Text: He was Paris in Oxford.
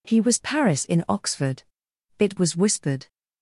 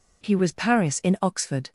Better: second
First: goes on to say "It was whispered"; noticeable; from 2.1 s on; 0.88 s long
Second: none

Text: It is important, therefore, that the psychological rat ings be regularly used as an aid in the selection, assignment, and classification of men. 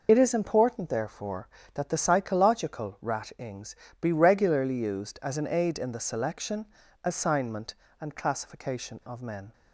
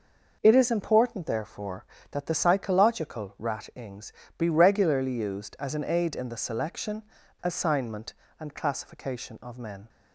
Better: second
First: loses the start of "It"; at 0.0 s; 60 ms // pauses between "ings" and "be"; slight; at 3.7 s; 0.24 s long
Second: pauses between "ings" and "be"; slight; at 4.1 s; 0.24 s long

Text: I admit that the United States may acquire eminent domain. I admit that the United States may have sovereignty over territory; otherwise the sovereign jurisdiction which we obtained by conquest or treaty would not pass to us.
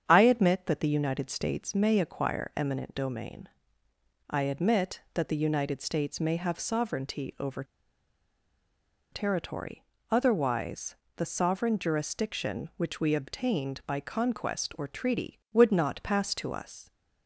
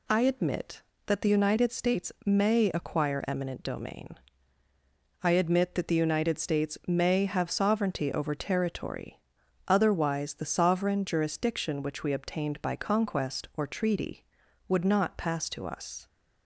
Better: second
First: starts louder than the rest; strong; until 1.0 s; 8 dB // pauses between "over" and "territory"; strong; at 7.6 s; 1.4 s long // pauses between "otherwise" and "the"; slight; at 10.9 s; 0.22 s long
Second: none

